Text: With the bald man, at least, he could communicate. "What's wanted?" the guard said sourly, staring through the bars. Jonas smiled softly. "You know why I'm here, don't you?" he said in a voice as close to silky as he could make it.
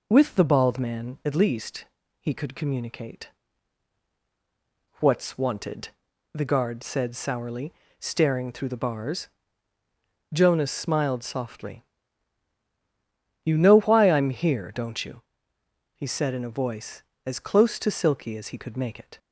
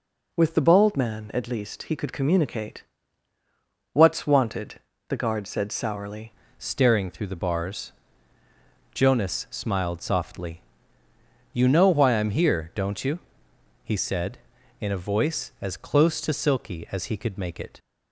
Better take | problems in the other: first | changes voice at "staring"; from 6.5 s on; 11.2 s long

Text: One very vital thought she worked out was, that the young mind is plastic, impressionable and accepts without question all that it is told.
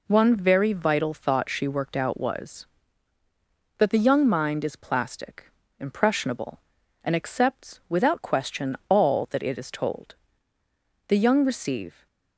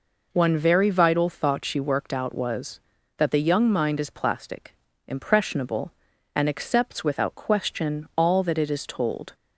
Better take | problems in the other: second | goes on to say "The young receive"; noticeable; from 11.0 s on; 1.0 s long

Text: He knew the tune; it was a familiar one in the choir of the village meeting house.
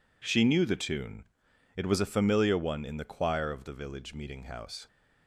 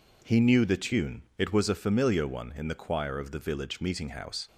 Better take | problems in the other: second | says "She" for "He"; at 0.2 s

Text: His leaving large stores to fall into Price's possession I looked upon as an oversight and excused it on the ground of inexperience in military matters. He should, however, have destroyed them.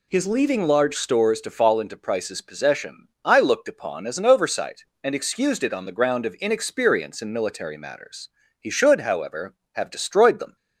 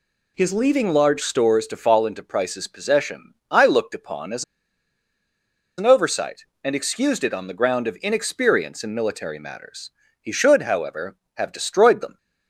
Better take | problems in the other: first | pauses between "as" and "an"; strong; at 4.4 s; 1.3 s long

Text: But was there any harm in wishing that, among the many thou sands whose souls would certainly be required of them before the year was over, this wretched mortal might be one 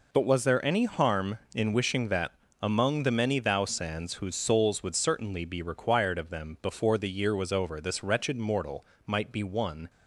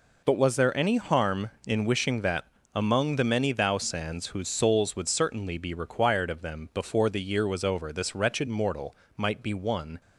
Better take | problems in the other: neither | pauses between "mortal" and "might"; slight; the same in both

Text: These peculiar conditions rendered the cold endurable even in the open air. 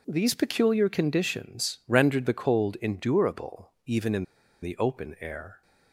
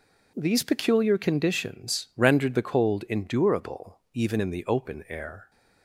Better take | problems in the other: second | pauses between "in" and "the"; at 4.2 s; 0.37 s long

